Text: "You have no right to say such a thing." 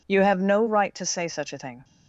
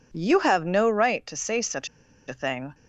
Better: first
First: none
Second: pauses between "such" and "a"; at 1.8 s; 0.40 s long

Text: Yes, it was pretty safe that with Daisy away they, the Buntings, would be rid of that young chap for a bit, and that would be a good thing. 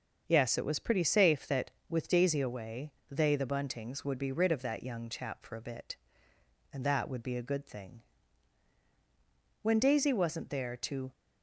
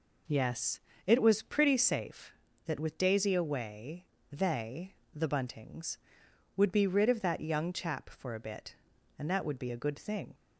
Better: second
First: starts louder than the rest; until 1.2 s; 6.5 dB // pauses between "away" and "they"; slight; at 2.9 s; 0.18 s long // goes on to say "When Daisy wasn't there to"; from 9.6 s on; 1.5 s long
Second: pauses between "away" and "they"; slight; at 4.0 s; 0.26 s long

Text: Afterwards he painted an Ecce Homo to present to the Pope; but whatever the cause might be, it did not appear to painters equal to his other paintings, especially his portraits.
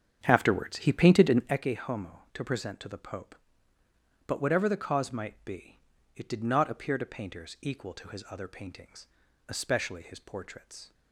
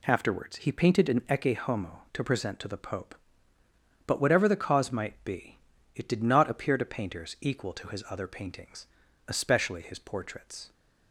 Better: second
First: starts louder than the rest; strong; until 1.6 s; 8 dB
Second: none

